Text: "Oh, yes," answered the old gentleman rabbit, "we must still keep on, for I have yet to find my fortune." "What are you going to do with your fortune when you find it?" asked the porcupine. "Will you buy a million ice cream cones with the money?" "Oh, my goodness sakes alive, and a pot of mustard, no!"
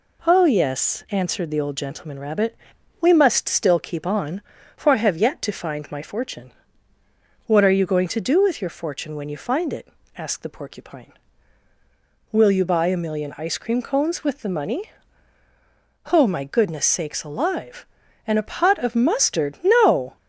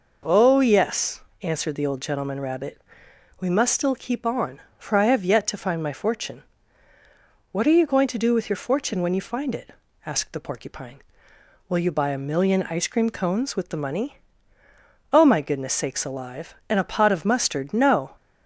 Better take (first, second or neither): neither